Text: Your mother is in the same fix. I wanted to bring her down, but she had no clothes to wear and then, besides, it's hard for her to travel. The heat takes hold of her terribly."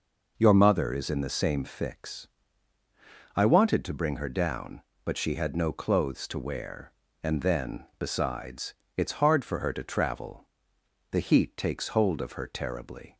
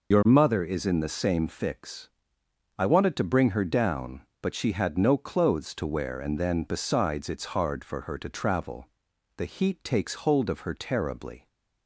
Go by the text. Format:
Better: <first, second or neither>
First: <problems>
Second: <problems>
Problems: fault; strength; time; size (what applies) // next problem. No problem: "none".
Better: first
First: none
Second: loses the start of "Your"; at 0.1 s; 55 ms